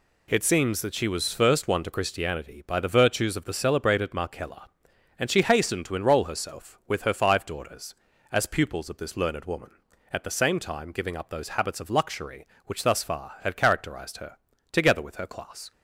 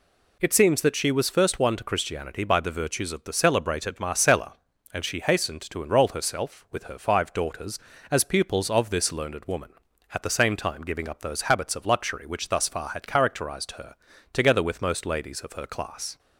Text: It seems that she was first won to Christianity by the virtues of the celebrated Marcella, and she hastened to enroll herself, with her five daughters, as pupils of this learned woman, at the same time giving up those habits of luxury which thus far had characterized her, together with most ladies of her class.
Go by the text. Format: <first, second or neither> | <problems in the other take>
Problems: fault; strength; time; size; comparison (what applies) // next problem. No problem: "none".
second | skips "most ladies of"; at 15.1 s